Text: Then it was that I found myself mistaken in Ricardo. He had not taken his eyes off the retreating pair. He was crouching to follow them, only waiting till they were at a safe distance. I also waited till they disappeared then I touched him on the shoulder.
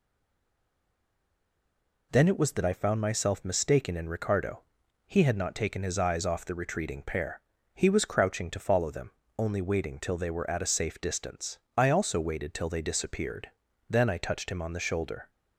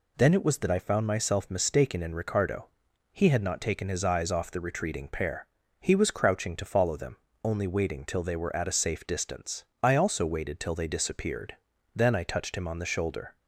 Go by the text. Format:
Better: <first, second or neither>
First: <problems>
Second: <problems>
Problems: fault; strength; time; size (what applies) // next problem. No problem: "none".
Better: second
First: stays silent before the first word; noticeable; until 2.1 s; 2.1 s long // pauses between "disappeared" and "then"; at 13.4 s; 0.40 s long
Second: pauses between "disappeared" and "then"; at 11.5 s; 0.40 s long